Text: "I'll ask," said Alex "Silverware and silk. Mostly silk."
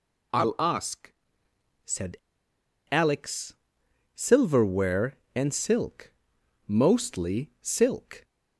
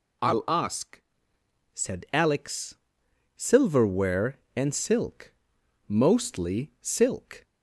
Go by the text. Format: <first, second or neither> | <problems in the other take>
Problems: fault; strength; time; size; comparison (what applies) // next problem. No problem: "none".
second | pauses between "said" and "Alex"; noticeable; at 2.1 s; 0.75 s long // pauses between "Alex" and "Silverware"; noticeable; at 3.5 s; 0.60 s long; noticeable in the second